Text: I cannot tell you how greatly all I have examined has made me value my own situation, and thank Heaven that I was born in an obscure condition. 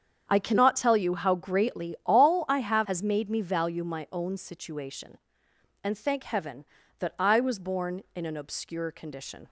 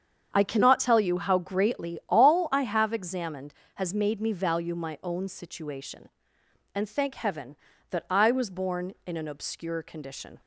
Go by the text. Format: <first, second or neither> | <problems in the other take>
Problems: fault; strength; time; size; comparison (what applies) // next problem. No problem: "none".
second | starts louder than the rest; strong; until 1.2 s; 8 dB; strong in the second // skips "examined"; at 2.8 s